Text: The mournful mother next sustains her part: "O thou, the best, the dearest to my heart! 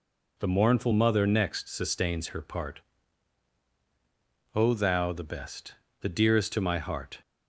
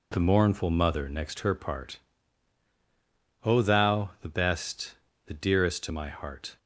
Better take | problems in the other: first | skips "sustains"; at 1.3 s

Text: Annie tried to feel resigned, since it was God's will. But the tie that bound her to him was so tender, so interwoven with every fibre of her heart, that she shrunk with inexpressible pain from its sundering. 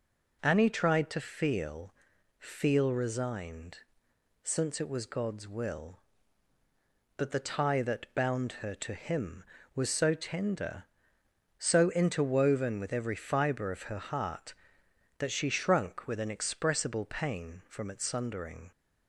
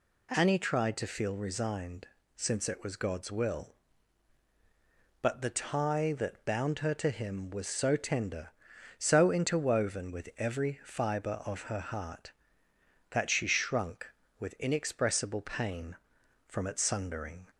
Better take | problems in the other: second | says "feel" twice; at 2.3 s

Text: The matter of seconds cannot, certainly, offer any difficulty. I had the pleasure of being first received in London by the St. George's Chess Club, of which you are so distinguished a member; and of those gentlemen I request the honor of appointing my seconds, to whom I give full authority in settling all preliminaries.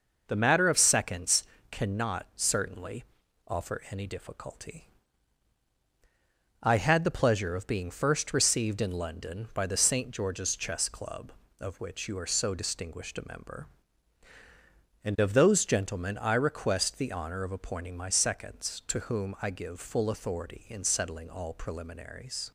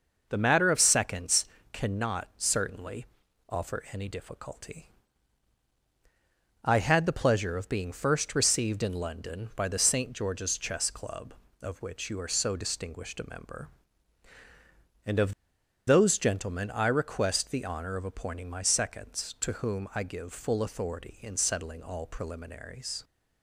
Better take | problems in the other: first | pauses between "seconds" and "cannot"; slight; at 1.4 s; 0.26 s long; slight in the first // pauses between "of" and "those"; noticeable; at 15.3 s; 0.55 s long

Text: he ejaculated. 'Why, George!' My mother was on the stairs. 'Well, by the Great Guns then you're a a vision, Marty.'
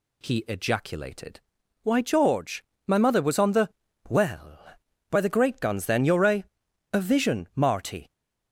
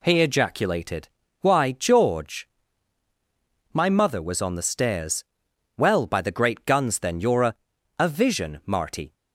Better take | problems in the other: second | skips "stairs"; at 3.8 s // pauses between "a" and "a"; noticeable; at 6.4 s; 0.50 s long; also in the second

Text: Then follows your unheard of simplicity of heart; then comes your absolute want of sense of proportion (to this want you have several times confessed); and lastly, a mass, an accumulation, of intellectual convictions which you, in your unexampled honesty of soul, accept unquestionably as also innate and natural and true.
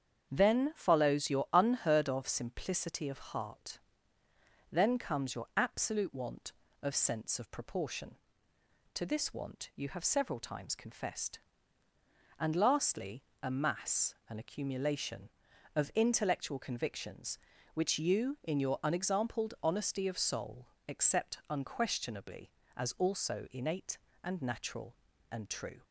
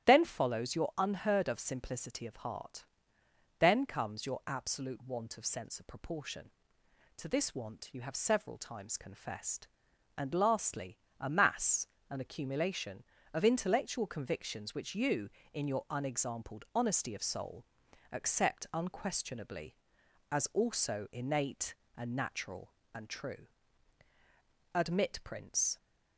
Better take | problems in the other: first | starts louder than the rest; strong; until 1.1 s; 11.5 dB; strong in the first // goes on to say "Admit prince"; noticeable; from 24.7 s on; 1.0 s long

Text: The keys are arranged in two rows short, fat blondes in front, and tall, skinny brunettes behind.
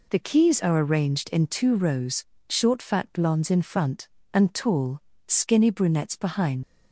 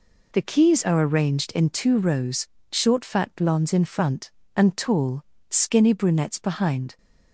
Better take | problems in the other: second | pauses between "rows" and "short"; slight; at 2.2 s; 0.26 s long; slight in the second // leaves "behind" unfinished; at 6.6 s; 110 ms

